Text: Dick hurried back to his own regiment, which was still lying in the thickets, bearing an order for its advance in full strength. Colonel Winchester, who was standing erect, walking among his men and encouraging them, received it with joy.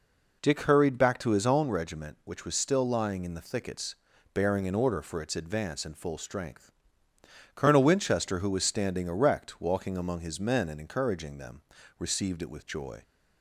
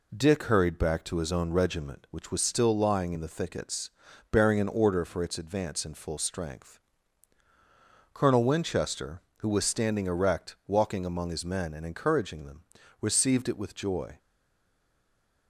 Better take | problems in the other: first | stays silent after the last word; noticeable; from 14.1 s on; 1.3 s long

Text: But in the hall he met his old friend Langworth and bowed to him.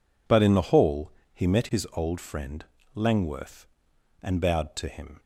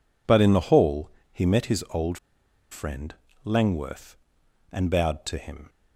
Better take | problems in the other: first | pauses between "hall" and "he"; slight; at 1.1 s; 0.20 s long; slight in the first // pauses between "old" and "friend"; noticeable; at 2.1 s; 0.54 s long // pauses between "friend" and "Langworth"; slight; at 3.1 s; 0.30 s long; slight in the first

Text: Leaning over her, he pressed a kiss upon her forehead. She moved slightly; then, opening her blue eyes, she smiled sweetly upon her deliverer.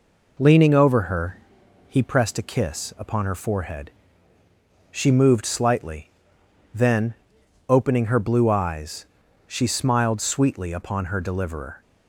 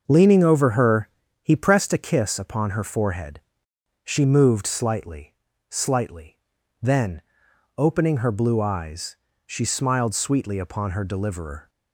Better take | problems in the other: first | starts louder than the rest; until 1.0 s; 6 dB // says "slightly" twice; at 5.6 s

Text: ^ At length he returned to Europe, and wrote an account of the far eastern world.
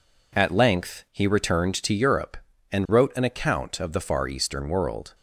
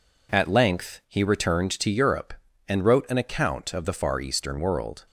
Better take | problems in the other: neither | none

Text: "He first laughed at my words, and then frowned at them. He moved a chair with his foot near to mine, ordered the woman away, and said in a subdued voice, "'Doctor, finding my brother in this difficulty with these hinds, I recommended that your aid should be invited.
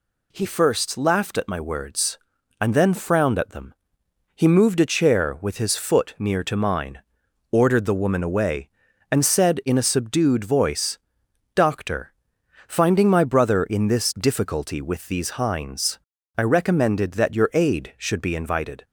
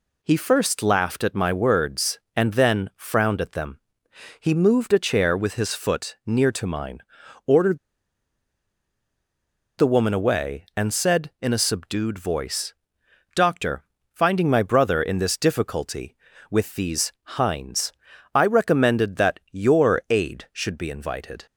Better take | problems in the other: first | pauses between "ordered" and "the"; strong; at 7.7 s; 2.0 s long

